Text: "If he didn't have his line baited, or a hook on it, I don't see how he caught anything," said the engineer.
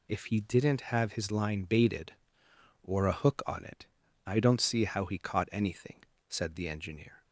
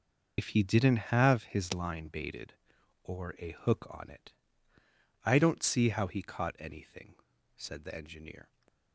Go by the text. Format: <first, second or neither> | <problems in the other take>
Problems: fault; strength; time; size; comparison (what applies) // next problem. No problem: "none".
first | loses the start of "If"; at 0.3 s; 85 ms